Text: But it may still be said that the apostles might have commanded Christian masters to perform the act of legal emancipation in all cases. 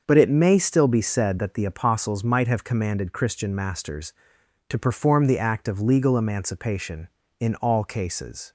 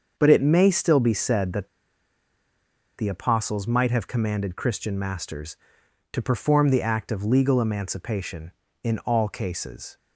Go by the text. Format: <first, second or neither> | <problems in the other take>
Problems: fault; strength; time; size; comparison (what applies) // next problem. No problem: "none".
first | starts louder than the rest; until 1.1 s; 6.5 dB; also in the first // pauses between "that" and "the"; strong; at 1.6 s; 1.3 s long